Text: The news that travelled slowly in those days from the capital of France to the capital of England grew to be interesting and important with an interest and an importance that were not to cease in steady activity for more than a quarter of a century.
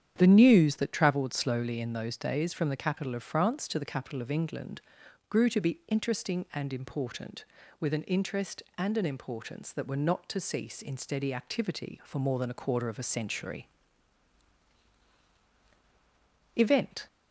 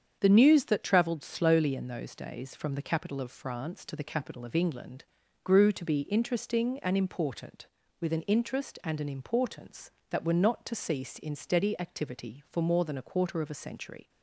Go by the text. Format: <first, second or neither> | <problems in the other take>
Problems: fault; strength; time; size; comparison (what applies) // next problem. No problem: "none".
second | starts louder than the rest; strong; until 1.1 s; 9 dB; strong in the second // pauses between "England" and "grew"; noticeable; at 4.8 s; 0.48 s long; also in the second // goes on to say "Event"; from 16.5 s on; 0.52 s long